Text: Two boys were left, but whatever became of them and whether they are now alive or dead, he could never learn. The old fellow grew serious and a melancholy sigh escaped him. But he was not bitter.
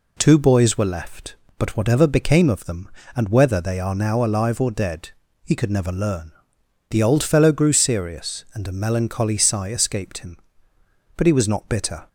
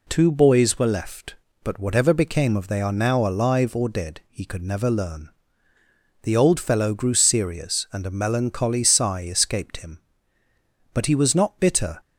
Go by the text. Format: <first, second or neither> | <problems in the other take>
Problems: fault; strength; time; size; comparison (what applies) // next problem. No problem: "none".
first | skips "them and whether"; at 2.6 s